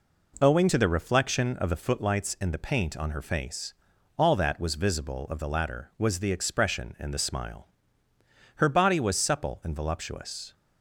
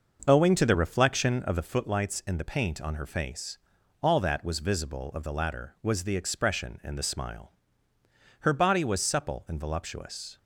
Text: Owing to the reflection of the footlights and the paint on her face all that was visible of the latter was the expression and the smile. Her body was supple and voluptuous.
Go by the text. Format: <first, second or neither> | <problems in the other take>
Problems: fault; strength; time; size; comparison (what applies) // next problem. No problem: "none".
first | starts louder than the rest; noticeable; until 1.6 s; 6 dB // pauses between "face" and "all"; at 3.5 s; 0.42 s long; also in the first